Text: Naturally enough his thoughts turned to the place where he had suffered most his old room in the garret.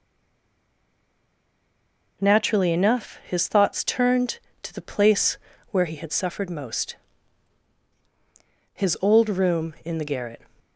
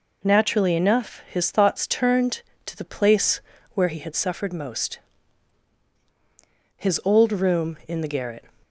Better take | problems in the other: second | stays silent before the first word; until 2.2 s; 2.2 s long // pauses between "place" and "where"; slight; at 5.3 s; 0.34 s long; slight in the second // pauses between "most" and "his"; strong; at 6.9 s; 1.7 s long; strong in the second

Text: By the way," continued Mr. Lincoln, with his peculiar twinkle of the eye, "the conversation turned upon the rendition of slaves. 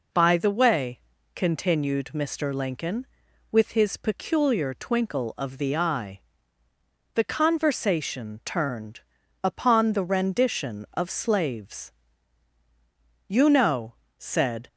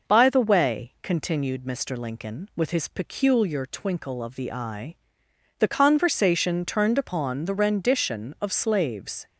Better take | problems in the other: second | pauses between "turned" and "upon"; at 8.9 s; 0.42 s long // goes on to say "You know said"; from 13.2 s on; 1.3 s long

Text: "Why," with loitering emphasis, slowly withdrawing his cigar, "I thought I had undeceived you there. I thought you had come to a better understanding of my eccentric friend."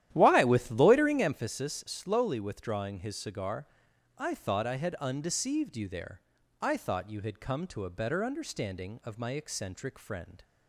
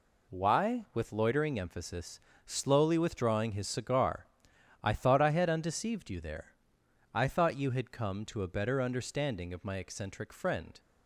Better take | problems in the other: second | starts louder than the rest; strong; until 1.4 s; 12 dB

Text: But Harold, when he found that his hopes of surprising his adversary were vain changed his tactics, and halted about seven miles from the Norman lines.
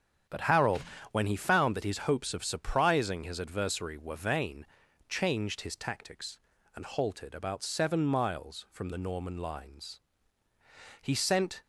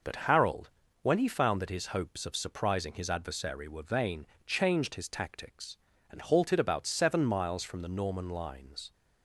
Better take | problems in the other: second | starts louder than the rest; strong; until 1.6 s; 8.5 dB // pauses between "vain" and "changed"; at 4.6 s; 0.42 s long; slight in the second // goes on to say "He sent"; from 11.0 s on; 0.60 s long

